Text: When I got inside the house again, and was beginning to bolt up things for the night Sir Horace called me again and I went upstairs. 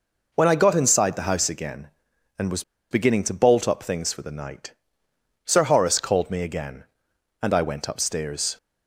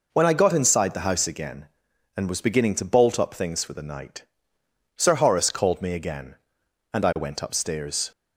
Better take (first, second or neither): second